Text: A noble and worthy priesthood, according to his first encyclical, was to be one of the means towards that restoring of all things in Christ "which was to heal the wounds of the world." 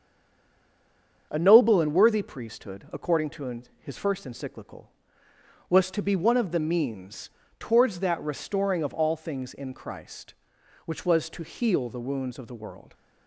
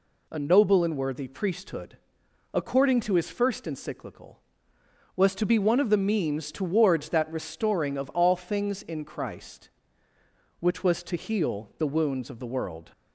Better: second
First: stays silent before the first word; noticeable; until 1.3 s; 1.3 s long // starts louder than the rest; strong; until 2.3 s; 7.5 dB // pauses between "to" and "his"; slight; at 3.6 s; 0.16 s long // pauses between "means" and "towards"; slight; at 7.2 s; 0.28 s long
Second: none

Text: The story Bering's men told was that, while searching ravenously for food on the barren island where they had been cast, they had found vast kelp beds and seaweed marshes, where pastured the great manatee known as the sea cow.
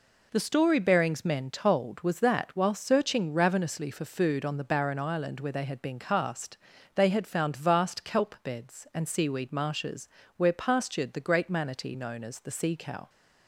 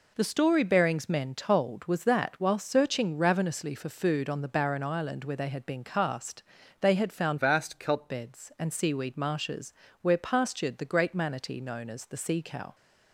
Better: first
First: none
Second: changes voice from "vast" to "kelp"; from 7.3 to 8.0 s; 0.7 s long

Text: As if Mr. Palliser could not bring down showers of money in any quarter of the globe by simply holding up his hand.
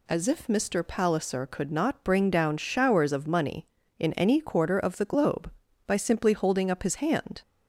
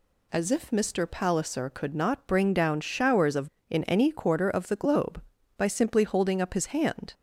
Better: first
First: none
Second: skips "money"; at 3.5 s

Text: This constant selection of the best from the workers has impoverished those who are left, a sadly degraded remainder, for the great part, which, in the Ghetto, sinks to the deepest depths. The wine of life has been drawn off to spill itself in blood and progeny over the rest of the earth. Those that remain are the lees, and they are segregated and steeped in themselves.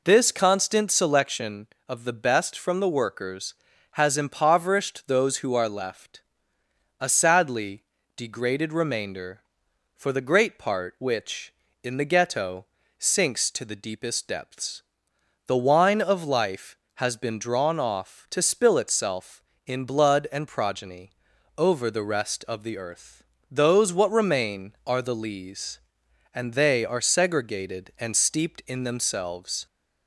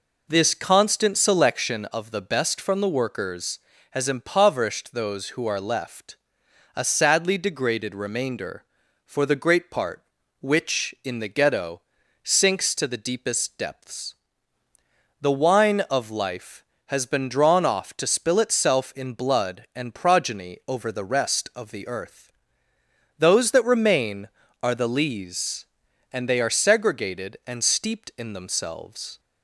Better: second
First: pauses between "sadly" and "degraded"; slight; at 7.8 s; 0.32 s long // pauses between "progeny" and "over"; noticeable; at 21.0 s; 0.48 s long // says "what" for "that"; at 23.9 s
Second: none

